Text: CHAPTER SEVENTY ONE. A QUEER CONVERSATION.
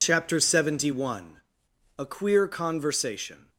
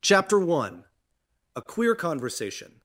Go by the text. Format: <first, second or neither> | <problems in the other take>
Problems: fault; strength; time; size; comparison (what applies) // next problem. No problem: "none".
first | skips "SEVENTY"; at 0.3 s